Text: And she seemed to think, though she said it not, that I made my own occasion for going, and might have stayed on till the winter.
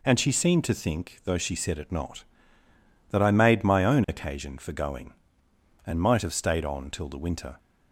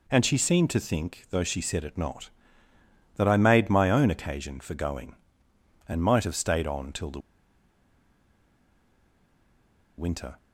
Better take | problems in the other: first | pauses between "the" and "winter"; strong; at 7.1 s; 2.7 s long

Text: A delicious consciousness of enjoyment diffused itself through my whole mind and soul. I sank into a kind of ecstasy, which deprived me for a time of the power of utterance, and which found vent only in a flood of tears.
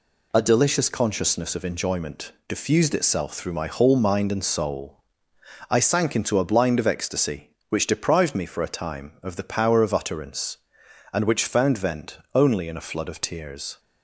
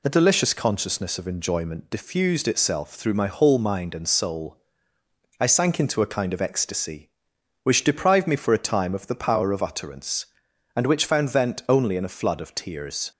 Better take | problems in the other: second | pauses between "enjoyment" and "diffused"; slight; at 2.2 s; 0.18 s long // says "blind" for "kind"; at 6.4 s

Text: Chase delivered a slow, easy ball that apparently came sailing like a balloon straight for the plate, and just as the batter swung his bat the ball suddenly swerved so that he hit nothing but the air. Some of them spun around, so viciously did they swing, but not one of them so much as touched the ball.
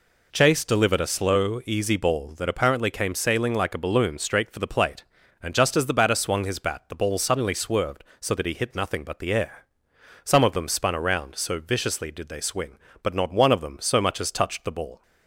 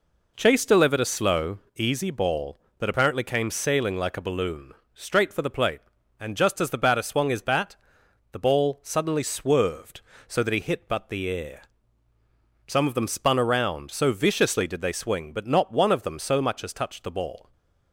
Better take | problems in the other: first | pauses between "balloon" and "straight"; slight; at 4.7 s; 0.22 s long // pauses between "bat" and "the"; noticeable; at 7.7 s; 0.56 s long // skips "nothing"; at 10.8 s // stays silent after the last word; slight; from 17.4 s on; 0.5 s long

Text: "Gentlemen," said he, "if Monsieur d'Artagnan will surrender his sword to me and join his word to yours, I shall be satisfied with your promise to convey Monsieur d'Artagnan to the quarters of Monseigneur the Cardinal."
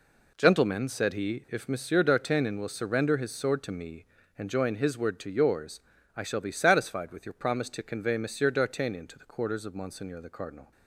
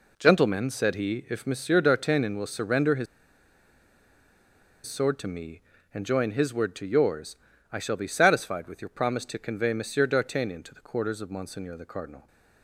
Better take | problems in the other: first | pauses between "his" and "sword"; strong; at 3.0 s; 1.8 s long

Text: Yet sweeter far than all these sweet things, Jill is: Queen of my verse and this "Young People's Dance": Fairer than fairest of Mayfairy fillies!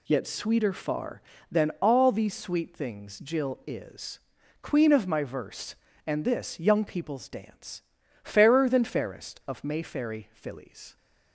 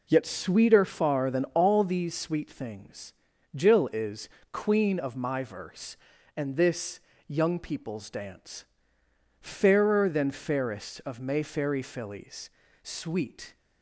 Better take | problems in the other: first | pauses between "this" and "Young"; slight; at 7.0 s; 0.26 s long // goes on to say "Sweet"; noticeable; from 12.8 s on; 0.72 s long

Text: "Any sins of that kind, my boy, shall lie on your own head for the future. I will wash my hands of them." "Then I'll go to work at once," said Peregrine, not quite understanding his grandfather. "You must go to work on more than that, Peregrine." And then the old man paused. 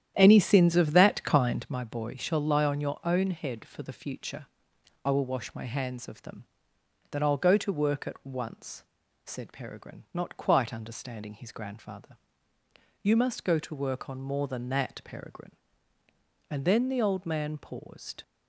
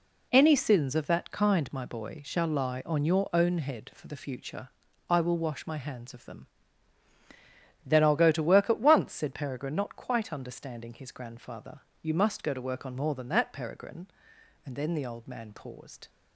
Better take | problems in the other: second | starts louder than the rest; strong; until 1.7 s; 10 dB

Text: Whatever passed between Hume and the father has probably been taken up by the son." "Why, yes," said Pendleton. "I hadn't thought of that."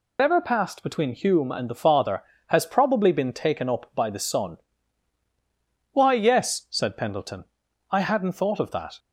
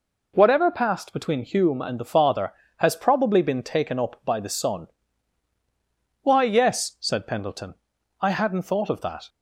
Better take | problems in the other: second | loses the start of "Whatever"; at 0.1 s; 150 ms

